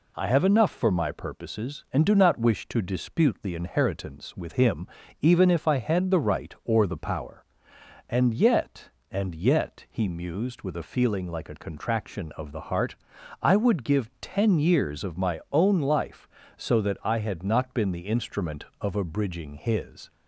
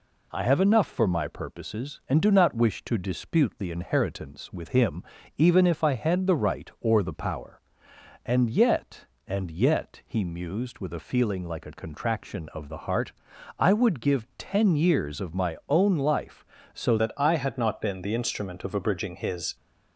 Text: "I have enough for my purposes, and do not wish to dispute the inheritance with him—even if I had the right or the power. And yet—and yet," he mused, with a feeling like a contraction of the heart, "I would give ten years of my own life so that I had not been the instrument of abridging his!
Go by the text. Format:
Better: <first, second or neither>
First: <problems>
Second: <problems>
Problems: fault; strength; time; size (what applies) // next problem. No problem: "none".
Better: first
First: none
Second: changes voice at "that"; from 16.9 s on; 2.6 s long